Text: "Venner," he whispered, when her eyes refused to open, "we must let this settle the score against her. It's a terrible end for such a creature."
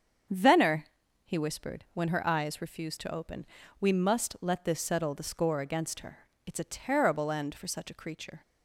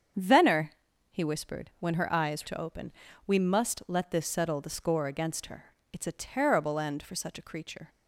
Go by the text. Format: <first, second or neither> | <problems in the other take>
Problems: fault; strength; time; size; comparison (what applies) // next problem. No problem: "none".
first | starts louder than the rest; strong; until 1.5 s; 7.5 dB; strong in the first // skips "refused"; at 2.4 s